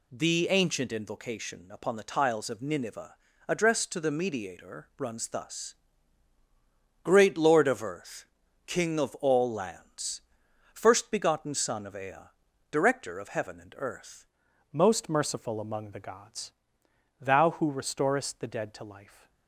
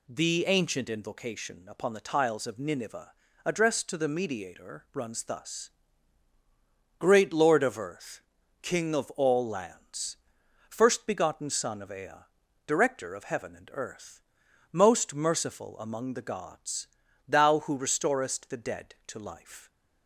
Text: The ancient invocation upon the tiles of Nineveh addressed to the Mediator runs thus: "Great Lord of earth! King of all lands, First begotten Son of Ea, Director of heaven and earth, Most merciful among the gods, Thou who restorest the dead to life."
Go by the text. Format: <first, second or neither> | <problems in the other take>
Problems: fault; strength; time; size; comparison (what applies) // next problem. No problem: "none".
second | pauses between "Nineveh" and "addressed"; slight; at 3.1 s; 0.34 s long; slight in the second // changes voice at "Most"; from 14.7 s on; 4.5 s long